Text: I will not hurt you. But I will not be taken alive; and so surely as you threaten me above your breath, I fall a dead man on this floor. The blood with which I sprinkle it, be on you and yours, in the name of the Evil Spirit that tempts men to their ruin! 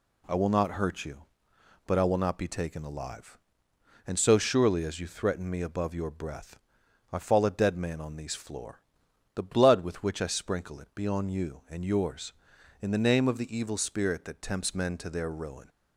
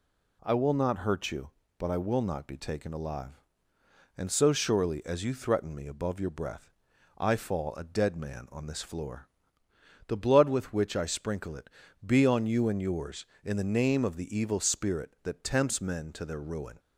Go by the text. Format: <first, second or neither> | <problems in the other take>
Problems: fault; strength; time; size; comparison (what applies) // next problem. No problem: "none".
second | says "these" for "this"; at 8.1 s